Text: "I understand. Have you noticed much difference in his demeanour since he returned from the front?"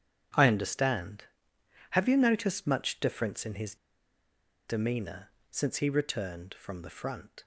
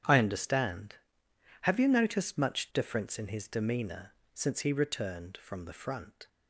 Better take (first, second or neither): second